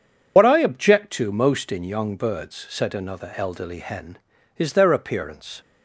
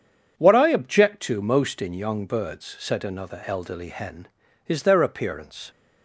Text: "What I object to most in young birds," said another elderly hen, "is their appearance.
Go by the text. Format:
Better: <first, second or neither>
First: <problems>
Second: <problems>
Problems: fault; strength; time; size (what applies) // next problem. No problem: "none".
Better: second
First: loses the start of "What"; at 0.3 s; 80 ms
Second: none